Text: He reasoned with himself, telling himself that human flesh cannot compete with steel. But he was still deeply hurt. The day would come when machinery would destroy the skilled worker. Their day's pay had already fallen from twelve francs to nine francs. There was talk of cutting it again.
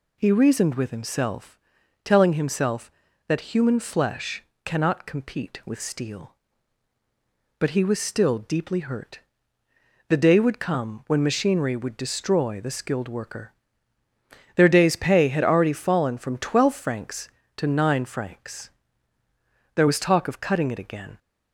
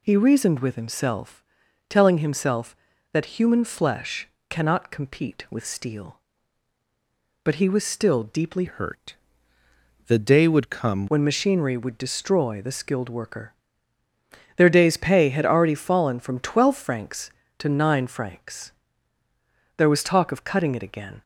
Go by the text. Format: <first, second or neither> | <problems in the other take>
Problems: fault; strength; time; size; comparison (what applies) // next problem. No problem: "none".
first | pauses between "flesh" and "cannot"; slight; at 4.2 s; 0.22 s long; slight in the first // changes voice from "hurt" to "come"; from 8.6 to 11.0 s; 2.4 s long